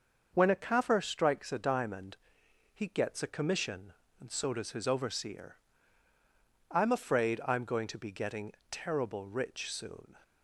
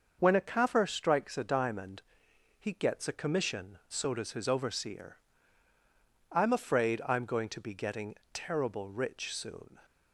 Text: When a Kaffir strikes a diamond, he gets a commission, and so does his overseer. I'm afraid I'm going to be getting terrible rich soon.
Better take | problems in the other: first | starts louder than the rest; until 1.2 s; 6.5 dB; also in the first // skips "and"; at 3.8 s // pauses between "getting" and "terrible"; slight; at 8.1 s; 0.18 s long; slight in the first

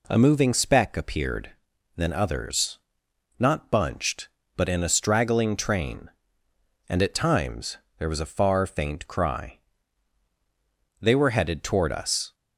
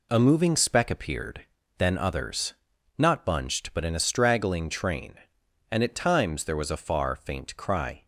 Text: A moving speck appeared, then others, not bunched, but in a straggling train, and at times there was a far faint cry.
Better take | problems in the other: second | pauses between "times" and "there"; slight; at 7.7 s; 0.20 s long // goes on to say "They were headed toward us"; from 11.0 s on; 1.3 s long

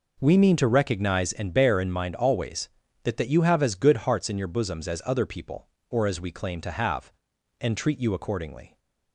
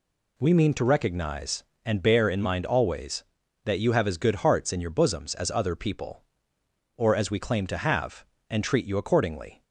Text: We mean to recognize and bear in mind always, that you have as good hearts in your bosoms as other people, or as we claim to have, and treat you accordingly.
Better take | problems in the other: second | says "that" twice; at 3.1 s

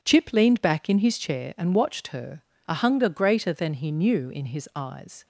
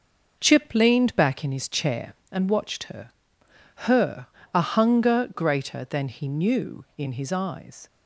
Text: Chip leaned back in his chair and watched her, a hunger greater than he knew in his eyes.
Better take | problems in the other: first | starts louder than the rest; noticeable; until 1.4 s; 6 dB // says "her" twice; at 3.8 s

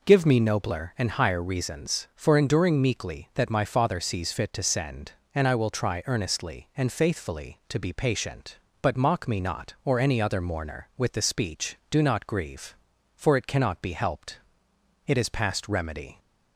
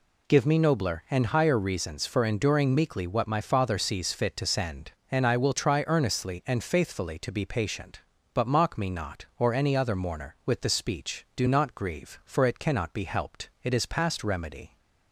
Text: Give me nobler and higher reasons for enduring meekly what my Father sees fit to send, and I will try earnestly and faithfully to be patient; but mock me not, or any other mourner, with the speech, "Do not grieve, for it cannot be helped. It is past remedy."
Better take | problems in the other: second | says "that" for "what"; at 3.3 s

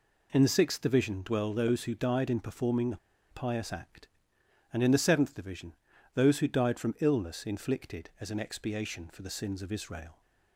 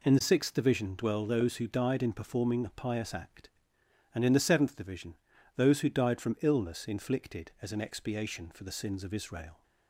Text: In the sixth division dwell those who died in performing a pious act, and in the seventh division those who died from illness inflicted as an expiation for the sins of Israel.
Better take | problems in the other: second | pauses between "a" and "pious"; slight; at 2.9 s; 0.32 s long // pauses between "division" and "those"; at 5.7 s; 0.40 s long; also in the second

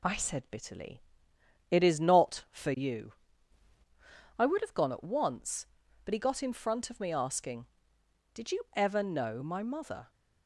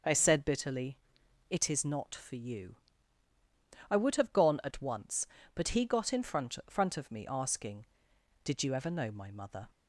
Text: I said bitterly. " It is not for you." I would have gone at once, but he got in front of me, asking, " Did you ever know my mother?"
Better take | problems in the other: first | says "front" twice; at 6.6 s

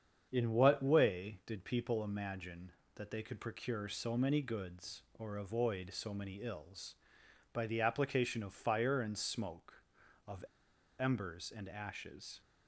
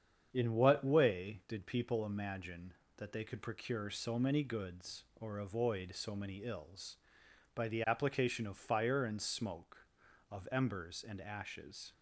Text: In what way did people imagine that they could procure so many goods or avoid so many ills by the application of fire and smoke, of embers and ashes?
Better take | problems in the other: second | starts louder than the rest; strong; until 1.3 s; 7.5 dB; strong in the second // pauses between "of" and "embers"; noticeable; at 10.4 s; 0.54 s long

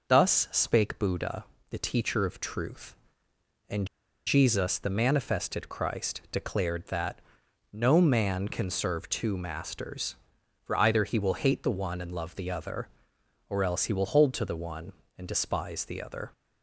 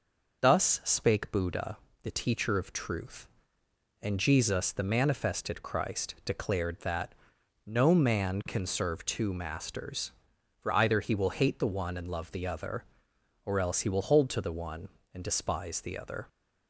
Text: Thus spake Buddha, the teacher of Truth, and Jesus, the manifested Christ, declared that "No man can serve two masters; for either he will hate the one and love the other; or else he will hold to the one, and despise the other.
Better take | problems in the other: second | pauses between "and" and "Jesus"; at 3.8 s; 0.39 s long // pauses between "that" and "No"; noticeable; at 7.2 s; 0.50 s long; noticeable in the second

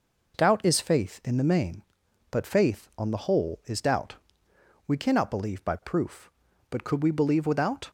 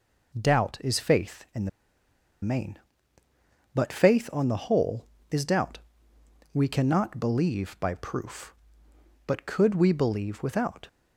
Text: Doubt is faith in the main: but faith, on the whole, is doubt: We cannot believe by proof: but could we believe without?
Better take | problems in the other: first | pauses between "the" and "main"; noticeable; at 1.6 s; 0.73 s long

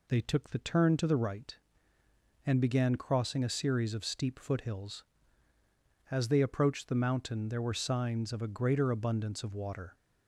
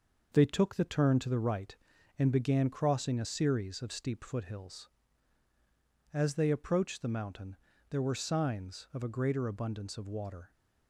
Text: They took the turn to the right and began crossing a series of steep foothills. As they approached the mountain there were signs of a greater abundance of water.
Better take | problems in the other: first | gets quieter; noticeable; throughout; 5 dB // pauses between "mountain" and "there"; slight; at 7.5 s; 0.32 s long

